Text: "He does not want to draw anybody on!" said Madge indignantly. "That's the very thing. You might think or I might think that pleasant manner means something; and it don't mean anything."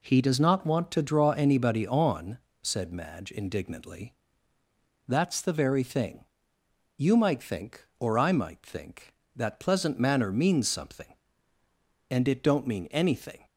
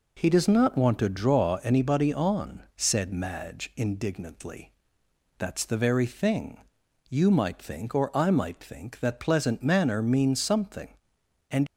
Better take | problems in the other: first | stops before "it don't mean anything"; at 11.6 s

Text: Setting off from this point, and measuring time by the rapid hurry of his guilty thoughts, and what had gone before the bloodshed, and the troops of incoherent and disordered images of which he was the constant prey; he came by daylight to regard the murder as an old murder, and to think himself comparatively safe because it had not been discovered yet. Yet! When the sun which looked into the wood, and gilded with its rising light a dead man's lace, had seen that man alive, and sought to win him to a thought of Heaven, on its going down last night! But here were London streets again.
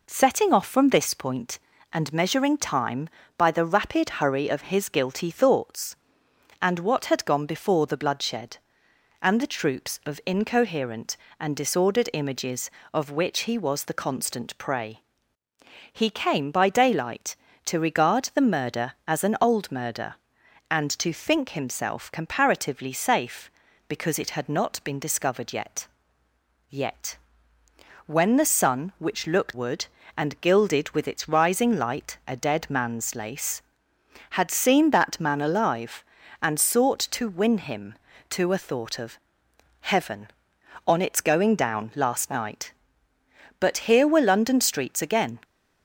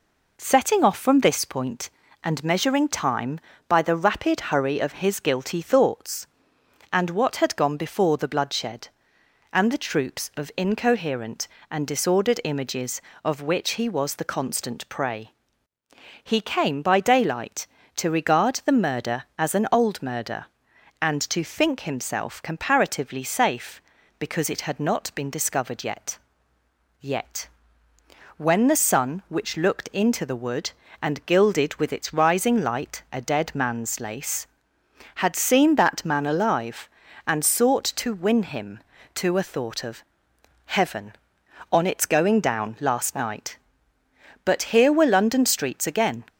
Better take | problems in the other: second | skips "into the"; at 29.5 s // pauses between "of" and "Heaven"; noticeable; at 39.1 s; 0.64 s long; noticeable in the second

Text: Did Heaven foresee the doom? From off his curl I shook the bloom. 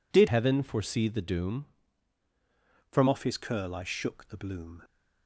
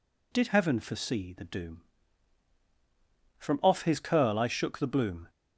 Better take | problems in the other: second | changes voice from "Heaven" to "From"; from 0.2 to 3.0 s; 2.8 s long

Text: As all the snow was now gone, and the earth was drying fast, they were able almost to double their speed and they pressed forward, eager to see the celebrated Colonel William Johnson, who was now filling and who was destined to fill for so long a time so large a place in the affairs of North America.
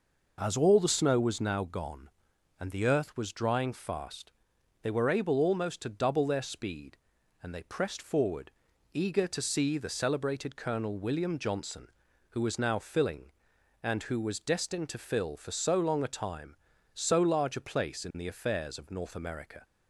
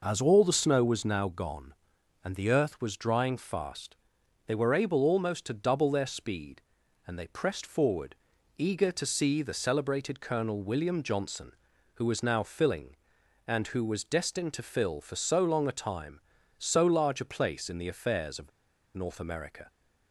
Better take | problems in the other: first | pauses between "of" and "North"; at 18.5 s; 0.45 s long

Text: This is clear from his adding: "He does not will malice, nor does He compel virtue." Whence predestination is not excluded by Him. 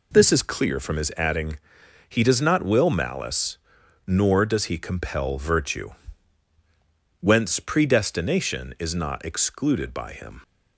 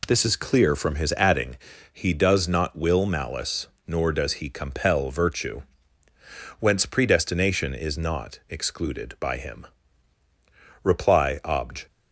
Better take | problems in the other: first | goes on to say "Reply Obj"; noticeable; from 10.8 s on; 1.0 s long

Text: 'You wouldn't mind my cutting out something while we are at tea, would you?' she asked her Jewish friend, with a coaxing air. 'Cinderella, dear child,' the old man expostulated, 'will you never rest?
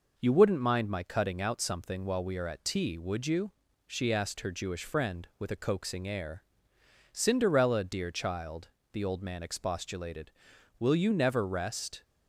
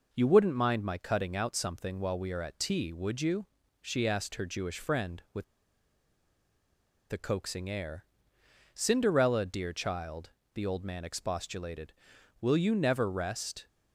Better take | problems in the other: first | pauses between "with" and "a"; strong; at 5.4 s; 1.6 s long

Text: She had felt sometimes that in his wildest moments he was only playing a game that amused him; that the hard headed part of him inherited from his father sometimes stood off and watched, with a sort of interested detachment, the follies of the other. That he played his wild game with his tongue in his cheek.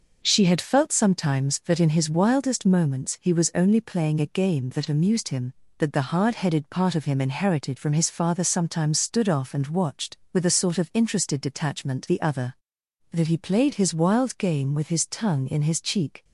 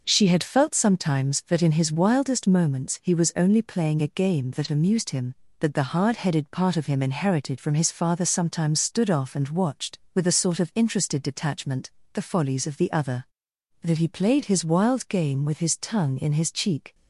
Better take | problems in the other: second | skips "the follies of"; at 12.0 s

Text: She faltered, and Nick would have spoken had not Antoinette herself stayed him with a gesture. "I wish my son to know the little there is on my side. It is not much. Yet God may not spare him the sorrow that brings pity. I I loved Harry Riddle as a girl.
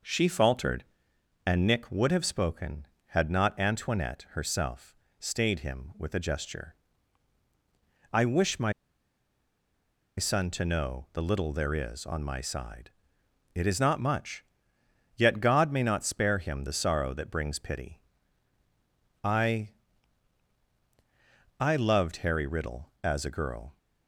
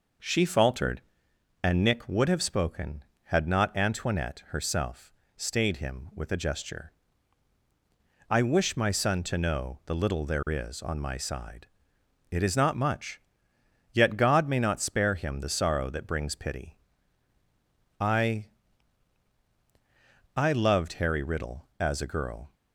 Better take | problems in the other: second | pauses between "herself" and "stayed"; slight; at 4.9 s; 0.22 s long; slight in the second // pauses between "my" and "son"; strong; at 8.7 s; 1.4 s long // pauses between "I" and "I"; strong; at 19.6 s; 1.9 s long; strong in the second

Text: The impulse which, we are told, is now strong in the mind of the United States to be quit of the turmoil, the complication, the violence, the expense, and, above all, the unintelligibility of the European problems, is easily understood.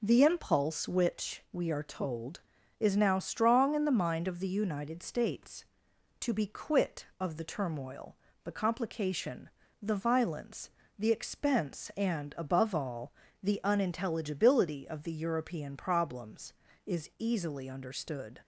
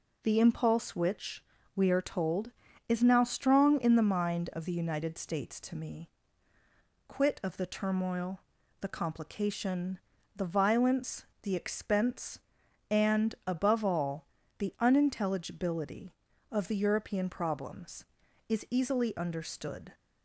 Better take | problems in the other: first | says "me" for "be"; at 5.7 s

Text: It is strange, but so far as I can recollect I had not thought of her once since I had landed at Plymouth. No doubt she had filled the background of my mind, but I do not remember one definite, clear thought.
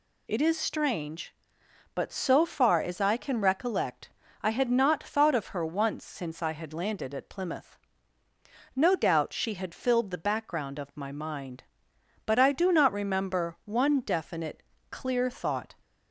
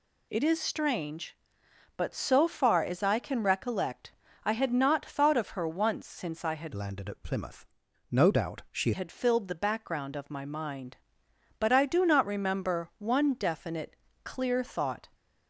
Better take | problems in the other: first | pauses between "recollect" and "I"; slight; at 4.1 s; 0.34 s long; slight in the first // changes voice from "landed" to "she"; from 6.7 to 8.9 s; 2.2 s long

